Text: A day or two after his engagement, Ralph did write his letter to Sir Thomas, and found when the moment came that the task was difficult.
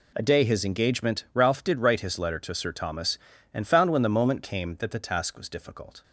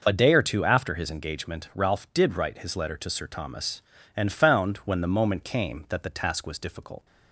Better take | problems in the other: second | skips "or two after"; at 0.4 s

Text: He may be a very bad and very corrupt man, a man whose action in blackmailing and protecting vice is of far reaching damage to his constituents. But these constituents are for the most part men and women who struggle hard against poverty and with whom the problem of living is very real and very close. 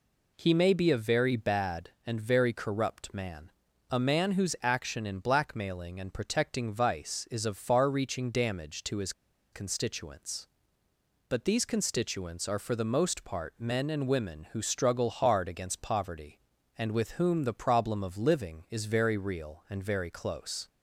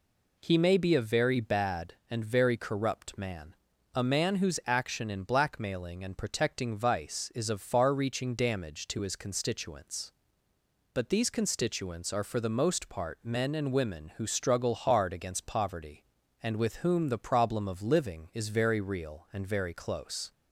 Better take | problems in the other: second | pauses between "his" and "constituents"; at 9.1 s; 0.40 s long

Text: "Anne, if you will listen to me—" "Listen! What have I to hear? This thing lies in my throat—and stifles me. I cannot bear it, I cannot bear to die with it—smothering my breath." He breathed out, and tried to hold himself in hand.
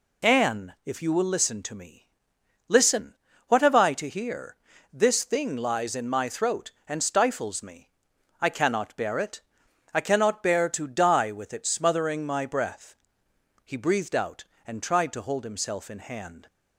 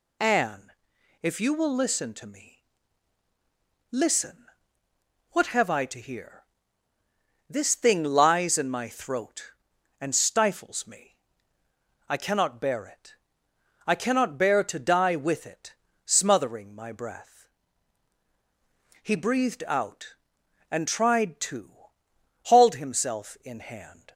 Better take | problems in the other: first | says "hauled" for "hold"; at 22.4 s

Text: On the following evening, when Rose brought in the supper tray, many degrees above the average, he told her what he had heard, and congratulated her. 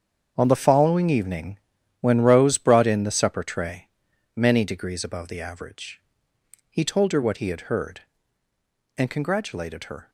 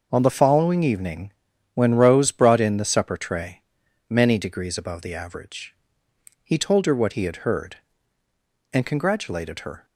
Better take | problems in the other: second | gets quieter; strong; throughout; 11.5 dB

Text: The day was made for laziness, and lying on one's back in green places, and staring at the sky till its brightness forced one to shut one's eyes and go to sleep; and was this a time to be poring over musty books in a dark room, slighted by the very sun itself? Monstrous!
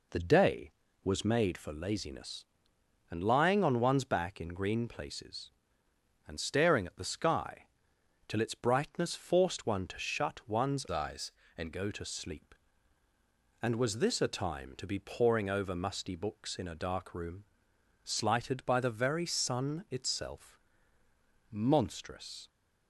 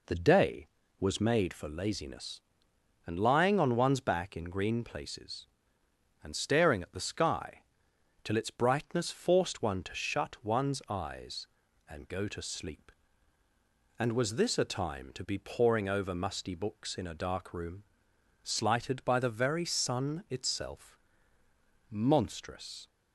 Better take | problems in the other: second | pauses between "sky" and "till"; noticeable; at 7.6 s; 0.60 s long; noticeable in the second // changes voice from "eyes" to "and"; from 10.9 to 11.7 s; 0.8 s long

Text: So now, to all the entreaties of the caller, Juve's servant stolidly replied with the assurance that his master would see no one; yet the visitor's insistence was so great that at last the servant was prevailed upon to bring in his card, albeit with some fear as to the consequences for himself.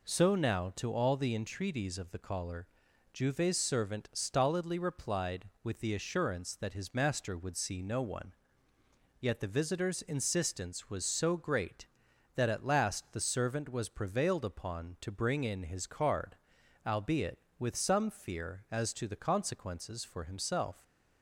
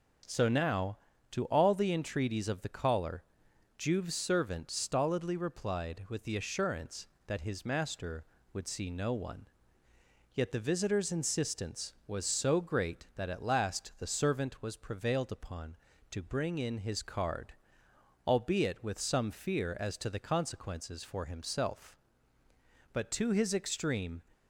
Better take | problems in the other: first | starts louder than the rest; until 1.6 s; 6.5 dB // goes on to say "But to his extreme"; noticeable; from 22.9 s on; 1.3 s long

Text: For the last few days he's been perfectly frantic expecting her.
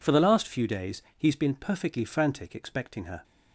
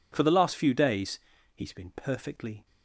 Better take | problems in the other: first | pauses between "days" and "he's"; at 1.1 s; 0.38 s long; slight in the first // stops before "frantic expecting her"; at 2.6 s

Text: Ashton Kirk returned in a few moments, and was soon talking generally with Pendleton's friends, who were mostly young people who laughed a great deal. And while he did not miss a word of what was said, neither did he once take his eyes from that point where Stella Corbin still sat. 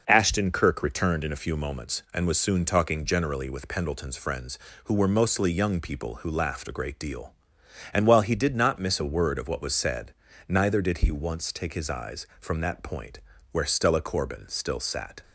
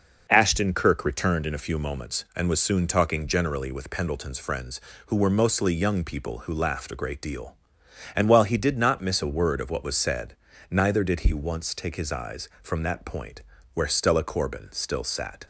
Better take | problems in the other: neither | pauses between "point" and "where"; slight; the same in both

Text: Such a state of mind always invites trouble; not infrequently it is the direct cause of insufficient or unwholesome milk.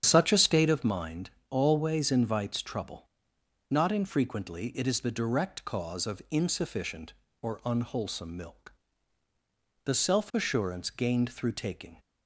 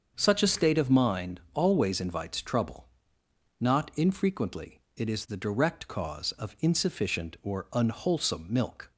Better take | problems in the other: second | starts louder than the rest; strong; until 1.0 s; 8.5 dB; also in the second // pauses between "mind" and "always"; slight; at 1.3 s; 0.18 s long // goes on to say "The self assurance gained through taking"; strong; from 9.8 s on; 2.1 s long

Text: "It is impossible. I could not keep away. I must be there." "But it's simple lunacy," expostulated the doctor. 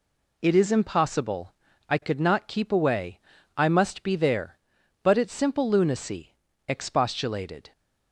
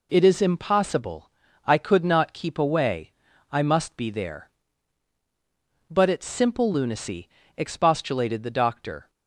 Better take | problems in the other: second | stops before "the doctor"; at 7.7 s

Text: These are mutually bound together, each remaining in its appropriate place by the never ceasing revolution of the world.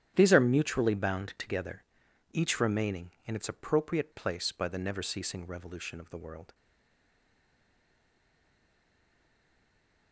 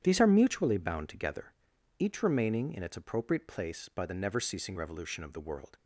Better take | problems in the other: second | starts louder than the rest; strong; until 1.1 s; 10.5 dB; strong in the second // stays silent after the last word; strong; from 6.5 s on; 3.6 s long

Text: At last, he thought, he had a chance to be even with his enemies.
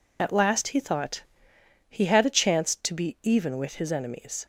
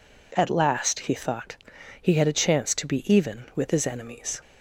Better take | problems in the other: second | loses the start of "At"; at 0.1 s; 35 ms

